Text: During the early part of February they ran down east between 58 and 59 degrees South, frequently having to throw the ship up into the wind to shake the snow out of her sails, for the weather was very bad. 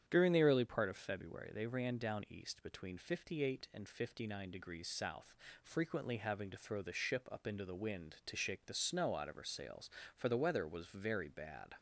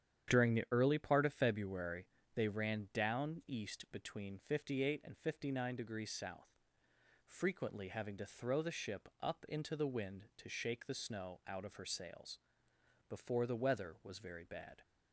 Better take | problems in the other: first | starts louder than the rest; strong; until 1.3 s; 9 dB; strong in the first // pauses between "February" and "they"; slight; at 2.0 s; 0.30 s long // says "before" for "for"; at 13.0 s

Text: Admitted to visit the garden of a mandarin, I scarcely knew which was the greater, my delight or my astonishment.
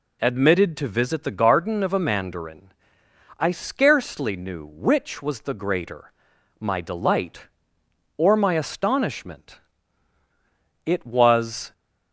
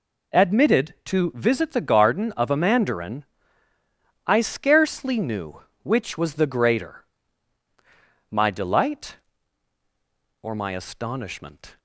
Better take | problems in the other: second | goes on to say "It was"; noticeable; from 10.8 s on; 0.88 s long

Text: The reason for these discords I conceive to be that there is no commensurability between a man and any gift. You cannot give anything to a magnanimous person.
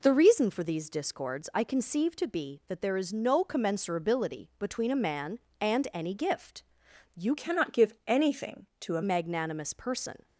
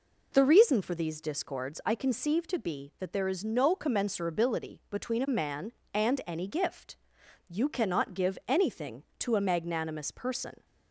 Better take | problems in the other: second | changes voice from "cannot" to "a"; from 7.3 to 9.0 s; 1.7 s long

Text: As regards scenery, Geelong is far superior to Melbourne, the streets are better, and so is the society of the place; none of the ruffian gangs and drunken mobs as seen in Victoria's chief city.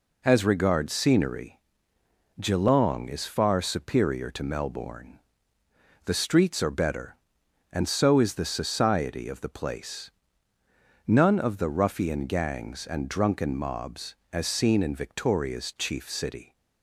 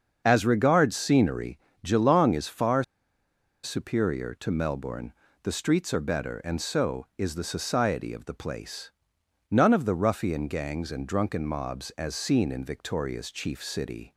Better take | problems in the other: first | starts louder than the rest; until 1.2 s; 6.5 dB // pauses between "far" and "superior"; noticeable; at 2.8 s; 0.79 s long

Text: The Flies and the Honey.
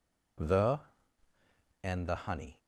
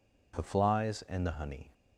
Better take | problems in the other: second | skips "Flies"; at 1.3 s

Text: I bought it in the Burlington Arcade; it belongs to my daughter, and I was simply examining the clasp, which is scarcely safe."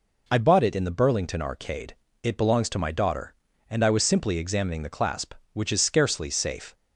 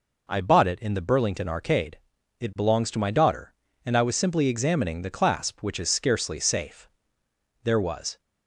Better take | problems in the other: first | goes on to say "There was"; from 7.6 s on; 0.56 s long

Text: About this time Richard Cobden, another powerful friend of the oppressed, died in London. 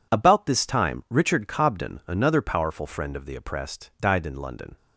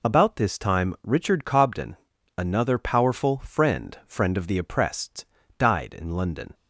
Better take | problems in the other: first | says "friend" twice; at 4.0 s

